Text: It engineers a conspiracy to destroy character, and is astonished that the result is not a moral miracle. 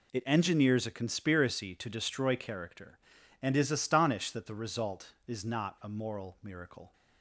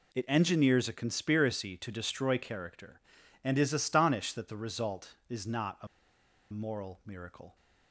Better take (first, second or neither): first